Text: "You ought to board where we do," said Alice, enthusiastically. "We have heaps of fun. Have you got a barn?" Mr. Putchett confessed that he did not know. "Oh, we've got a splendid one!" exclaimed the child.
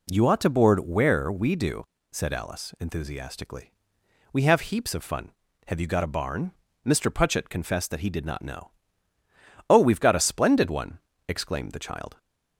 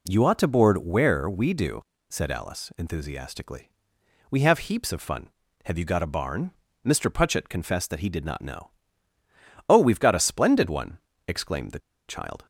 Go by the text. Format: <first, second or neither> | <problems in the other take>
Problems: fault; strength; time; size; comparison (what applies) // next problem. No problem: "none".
first | pauses between "the" and "child"; slight; at 11.8 s; 0.27 s long